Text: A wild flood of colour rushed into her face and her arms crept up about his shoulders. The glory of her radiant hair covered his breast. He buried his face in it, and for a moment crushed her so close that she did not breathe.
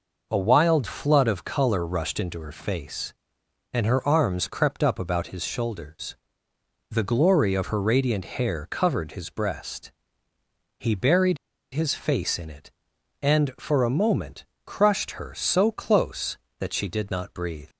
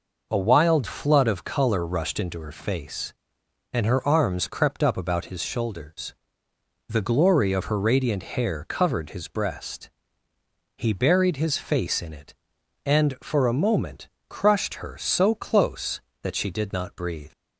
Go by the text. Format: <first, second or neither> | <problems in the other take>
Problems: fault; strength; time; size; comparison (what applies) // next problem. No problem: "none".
second | pauses between "buried" and "his"; slight; at 11.3 s; 0.36 s long // pauses between "moment" and "crushed"; slight; at 14.4 s; 0.20 s long; slight in the second